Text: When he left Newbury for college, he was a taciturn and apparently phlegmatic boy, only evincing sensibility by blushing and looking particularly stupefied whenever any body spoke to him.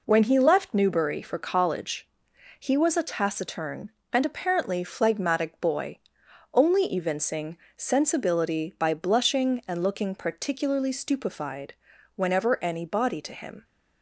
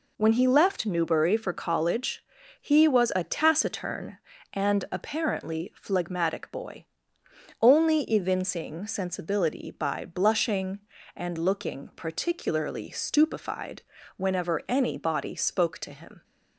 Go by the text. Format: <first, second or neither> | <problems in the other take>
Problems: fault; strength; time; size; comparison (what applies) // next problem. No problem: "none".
second | pauses between "evincing" and "sensibility"; slight; at 7.5 s; 0.22 s long // pauses between "stupefied" and "whenever"; at 11.7 s; 0.44 s long; slight in the second // skips "spoke"; at 13.2 s